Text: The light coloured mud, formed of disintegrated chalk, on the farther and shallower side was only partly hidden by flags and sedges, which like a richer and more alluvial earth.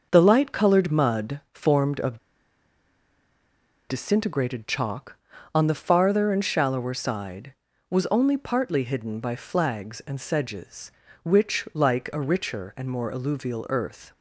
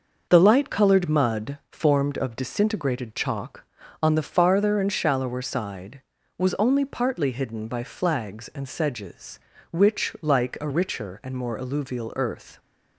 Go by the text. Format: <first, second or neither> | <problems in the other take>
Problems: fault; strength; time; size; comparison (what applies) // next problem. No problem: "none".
second | starts louder than the rest; noticeable; until 1.1 s; 6 dB; noticeable in the second // pauses between "of" and "disintegrated"; strong; at 2.1 s; 1.7 s long